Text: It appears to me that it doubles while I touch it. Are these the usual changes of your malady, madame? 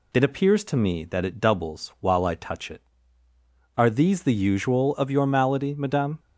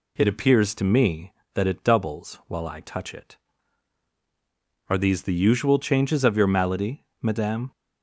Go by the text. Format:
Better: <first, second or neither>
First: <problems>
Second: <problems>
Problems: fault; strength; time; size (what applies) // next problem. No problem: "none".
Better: second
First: skips "changes"; at 4.9 s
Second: none